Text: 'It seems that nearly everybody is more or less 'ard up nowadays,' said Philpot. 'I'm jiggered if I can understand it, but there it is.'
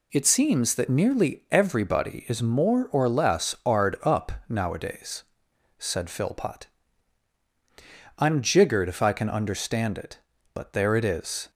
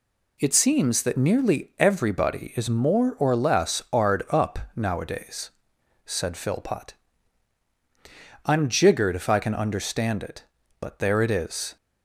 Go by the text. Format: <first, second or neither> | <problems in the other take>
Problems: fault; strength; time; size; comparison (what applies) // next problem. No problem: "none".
neither | pauses between "up" and "nowadays"; slight; the same in both